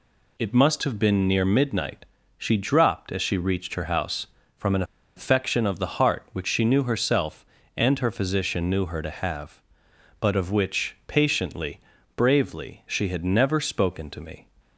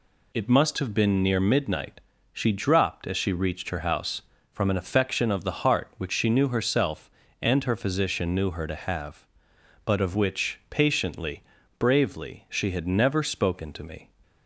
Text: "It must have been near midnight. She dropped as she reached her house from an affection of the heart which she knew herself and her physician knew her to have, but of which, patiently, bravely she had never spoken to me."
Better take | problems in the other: second | pauses between "an" and "affection"; slight; at 4.8 s; 0.33 s long

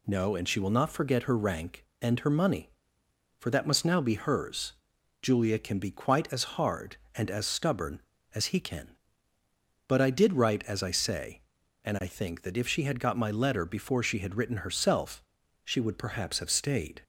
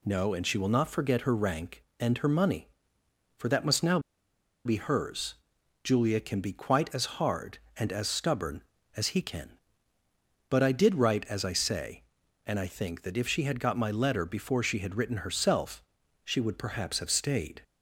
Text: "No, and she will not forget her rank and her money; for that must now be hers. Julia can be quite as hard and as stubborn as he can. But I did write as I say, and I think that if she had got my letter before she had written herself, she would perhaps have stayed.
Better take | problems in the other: first | pauses between "now" and "be"; noticeable; at 3.9 s; 0.65 s long

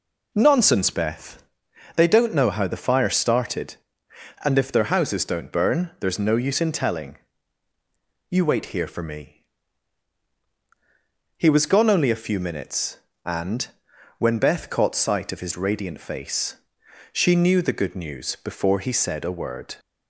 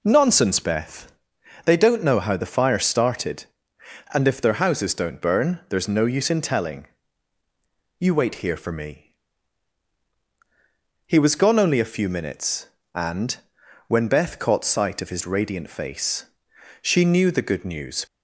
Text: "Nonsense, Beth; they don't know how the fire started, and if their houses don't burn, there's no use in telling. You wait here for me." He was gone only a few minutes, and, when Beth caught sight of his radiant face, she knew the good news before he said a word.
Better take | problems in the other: first | stops before "before he said a word"; at 18.0 s

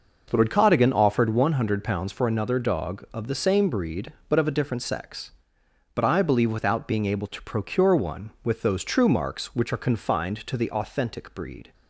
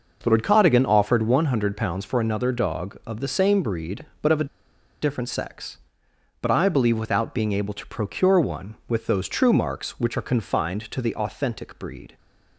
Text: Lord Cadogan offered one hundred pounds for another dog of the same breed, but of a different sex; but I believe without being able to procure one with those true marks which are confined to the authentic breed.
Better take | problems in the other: first | pauses between "a" and "different"; noticeable; at 4.4 s; 0.56 s long

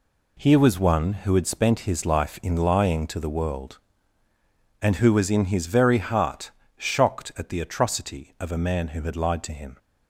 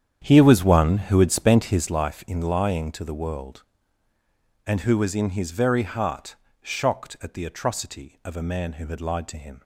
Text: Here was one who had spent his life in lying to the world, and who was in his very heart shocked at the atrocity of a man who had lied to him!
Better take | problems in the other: first | starts louder than the rest; strong; until 1.9 s; 9 dB // pauses between "heart" and "shocked"; slight; at 6.3 s; 0.24 s long; slight in the first

